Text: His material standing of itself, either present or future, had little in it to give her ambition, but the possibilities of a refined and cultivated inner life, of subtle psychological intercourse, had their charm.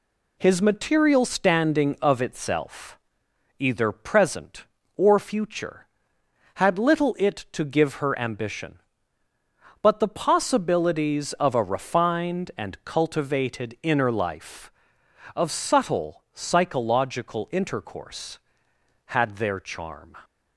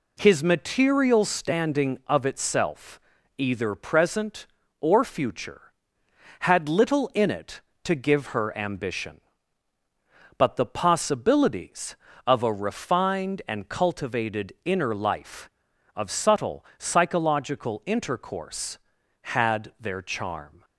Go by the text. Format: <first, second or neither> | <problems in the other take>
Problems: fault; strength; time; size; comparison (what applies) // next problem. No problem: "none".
second | skips "in"; at 7.1 s